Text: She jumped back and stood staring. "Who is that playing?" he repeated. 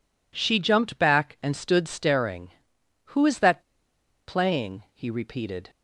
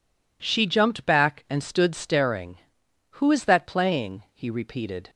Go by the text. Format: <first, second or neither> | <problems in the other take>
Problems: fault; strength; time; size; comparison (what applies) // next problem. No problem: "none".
second | pauses between "that" and "playing"; noticeable; at 3.6 s; 0.65 s long